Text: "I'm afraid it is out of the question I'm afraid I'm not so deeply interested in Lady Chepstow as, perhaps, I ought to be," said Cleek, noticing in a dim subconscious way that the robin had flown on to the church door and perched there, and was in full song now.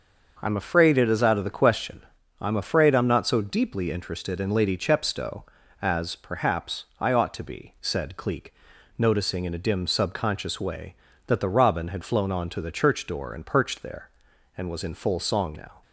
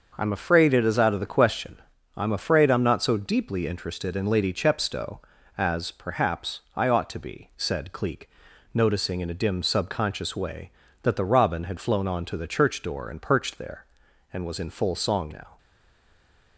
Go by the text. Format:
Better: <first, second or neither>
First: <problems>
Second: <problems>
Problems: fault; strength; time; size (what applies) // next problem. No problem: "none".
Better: first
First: starts louder than the rest; noticeable; until 1.4 s; 6 dB // pauses between "question" and "I'm"; at 2.0 s; 0.38 s long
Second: starts louder than the rest; noticeable; until 1.1 s; 6 dB // pauses between "question" and "I'm"; at 1.7 s; 0.38 s long // stays silent after the last word; from 15.5 s on; 1.0 s long